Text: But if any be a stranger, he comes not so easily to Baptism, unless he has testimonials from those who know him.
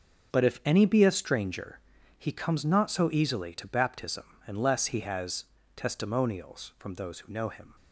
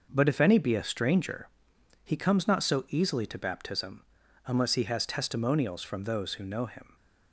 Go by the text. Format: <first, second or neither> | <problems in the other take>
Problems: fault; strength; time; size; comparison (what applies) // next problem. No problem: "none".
second | gets quieter; strong; throughout; 10.5 dB // pauses between "has" and "testimonials"; slight; at 5.4 s; 0.30 s long